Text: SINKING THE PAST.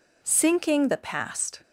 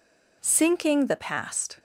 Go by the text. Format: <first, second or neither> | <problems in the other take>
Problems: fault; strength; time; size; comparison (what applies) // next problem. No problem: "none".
neither | none